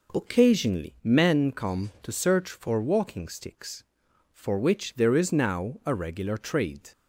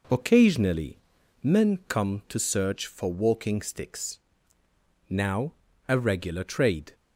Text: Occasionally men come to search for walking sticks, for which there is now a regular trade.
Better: first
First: none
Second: pauses between "Occasionally" and "men"; at 0.9 s; 0.42 s long // skips "for which there is"; at 4.6 s // pauses between "now" and "a"; slight; at 5.5 s; 0.34 s long

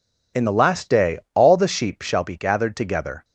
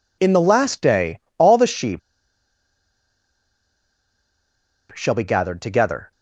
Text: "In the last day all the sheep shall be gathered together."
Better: first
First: pauses between "day" and "all"; slight; at 1.1 s; 0.16 s long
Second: pauses between "day" and "all"; slight; at 1.2 s; 0.18 s long // pauses between "sheep" and "shall"; strong; at 2.0 s; 2.9 s long

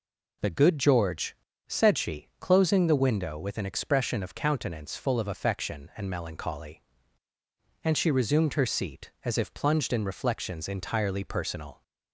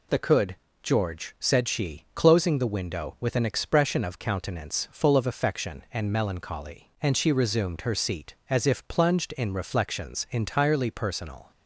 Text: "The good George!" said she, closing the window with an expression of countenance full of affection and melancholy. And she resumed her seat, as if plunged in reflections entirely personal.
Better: first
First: none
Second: says "could" for "good"; at 0.1 s

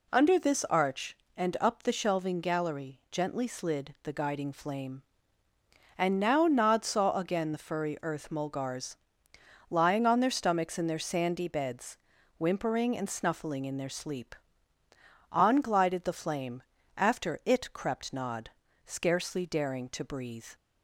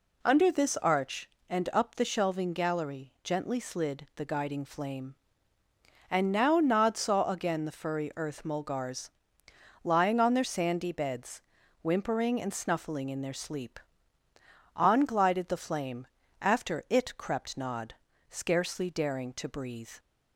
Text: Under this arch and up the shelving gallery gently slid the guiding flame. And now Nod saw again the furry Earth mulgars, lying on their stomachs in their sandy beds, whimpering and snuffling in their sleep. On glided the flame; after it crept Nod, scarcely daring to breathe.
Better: first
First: none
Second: skips "stomachs in their"; at 10.4 s

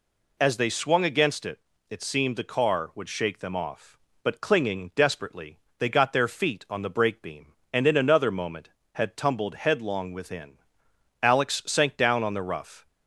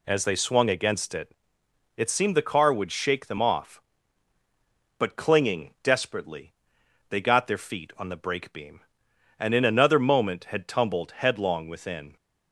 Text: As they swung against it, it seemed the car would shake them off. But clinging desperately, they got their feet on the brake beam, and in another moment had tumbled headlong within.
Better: second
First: goes on to say "Alex sank down on the rough"; from 11.2 s on; 1.6 s long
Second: none

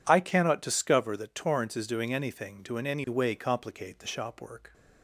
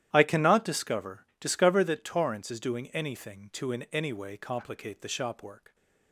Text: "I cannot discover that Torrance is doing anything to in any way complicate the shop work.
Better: first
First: none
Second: starts louder than the rest; strong; until 1.1 s; 11.5 dB // says "discover" twice; at 1.3 s

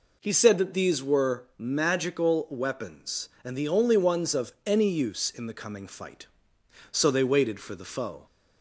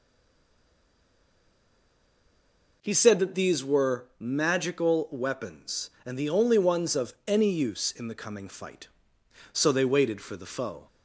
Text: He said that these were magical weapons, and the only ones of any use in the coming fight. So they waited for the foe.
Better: first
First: none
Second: stays silent before the first word; strong; until 2.8 s; 2.8 s long

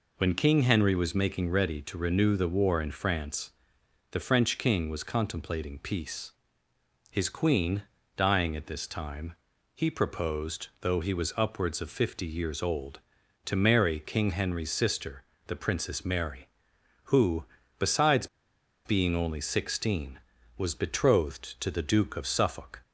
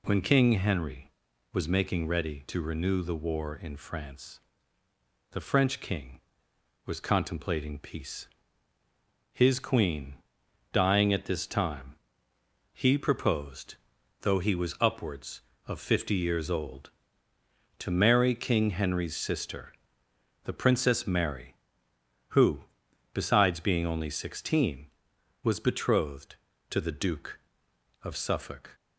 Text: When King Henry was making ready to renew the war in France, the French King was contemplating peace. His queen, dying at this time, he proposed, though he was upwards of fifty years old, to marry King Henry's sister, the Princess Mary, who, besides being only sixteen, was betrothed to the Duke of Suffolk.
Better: second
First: pauses between "besides" and "being"; noticeable; at 18.2 s; 0.57 s long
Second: none

